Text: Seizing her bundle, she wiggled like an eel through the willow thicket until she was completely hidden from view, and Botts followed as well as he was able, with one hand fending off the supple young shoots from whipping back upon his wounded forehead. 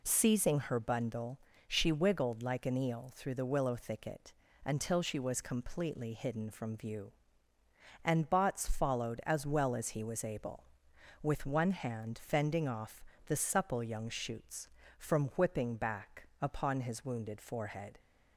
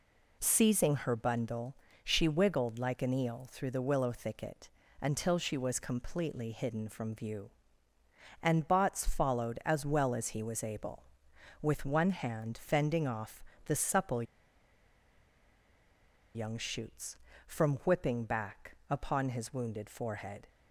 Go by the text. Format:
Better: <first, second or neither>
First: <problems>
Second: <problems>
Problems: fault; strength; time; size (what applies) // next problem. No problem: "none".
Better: first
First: pauses between "thicket" and "until"; slight; at 4.3 s; 0.32 s long // pauses between "off" and "the"; slight; at 13.0 s; 0.22 s long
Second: pauses between "thicket" and "until"; slight; at 4.6 s; 0.32 s long // pauses between "off" and "the"; slight; at 13.4 s; 0.22 s long // pauses between "supple" and "young"; strong; at 14.2 s; 2.1 s long